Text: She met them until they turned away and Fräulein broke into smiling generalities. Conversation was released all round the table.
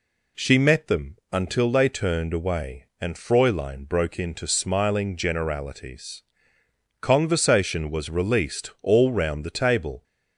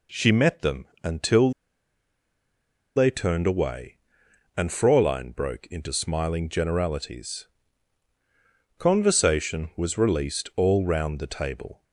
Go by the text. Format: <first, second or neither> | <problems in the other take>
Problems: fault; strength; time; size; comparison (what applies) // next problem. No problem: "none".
first | pauses between "them" and "until"; slight; at 0.8 s; 0.18 s long // pauses between "until" and "they"; strong; at 1.5 s; 1.4 s long